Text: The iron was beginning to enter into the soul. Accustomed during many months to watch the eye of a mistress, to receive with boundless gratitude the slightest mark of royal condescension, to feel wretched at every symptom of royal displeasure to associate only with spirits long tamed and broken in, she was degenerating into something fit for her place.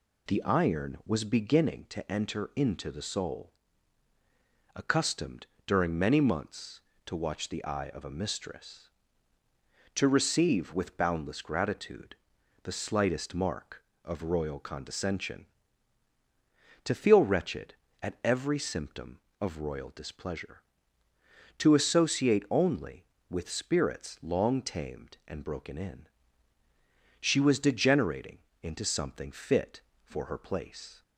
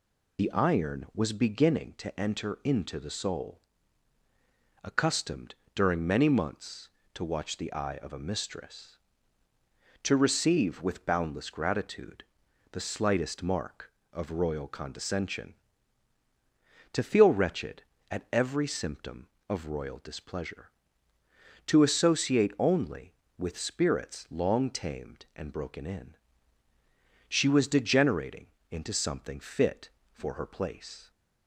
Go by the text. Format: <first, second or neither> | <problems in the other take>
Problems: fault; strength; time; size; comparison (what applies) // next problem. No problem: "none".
first | loses the start of "The"; at 0.3 s; 30 ms // pauses between "Accustomed" and "during"; slight; at 5.5 s; 0.22 s long; slight in the first // pauses between "gratitude" and "the"; noticeable; at 12.2 s; 0.48 s long; noticeable in the first // pauses between "degenerating" and "into"; slight; at 28.4 s; 0.24 s long; slight in the first